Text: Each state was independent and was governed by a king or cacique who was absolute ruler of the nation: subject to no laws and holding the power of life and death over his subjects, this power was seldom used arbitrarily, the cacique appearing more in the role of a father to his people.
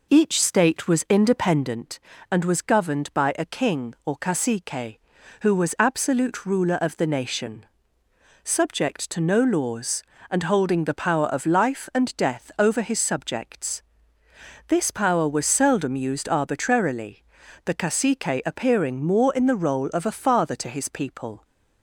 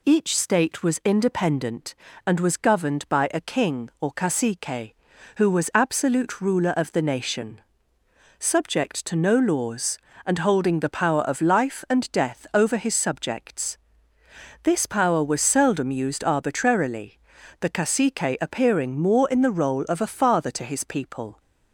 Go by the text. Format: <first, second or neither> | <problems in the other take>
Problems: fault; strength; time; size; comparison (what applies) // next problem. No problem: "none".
second | starts louder than the rest; noticeable; until 1.7 s; 4.5 dB